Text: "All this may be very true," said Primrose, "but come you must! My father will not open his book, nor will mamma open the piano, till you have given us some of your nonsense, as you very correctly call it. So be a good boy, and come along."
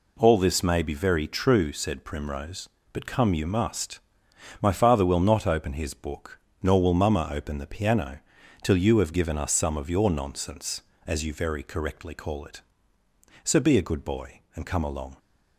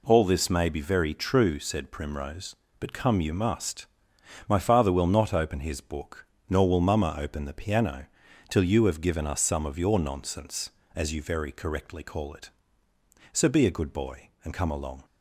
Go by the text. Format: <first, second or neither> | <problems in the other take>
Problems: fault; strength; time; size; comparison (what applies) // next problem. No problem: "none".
neither | none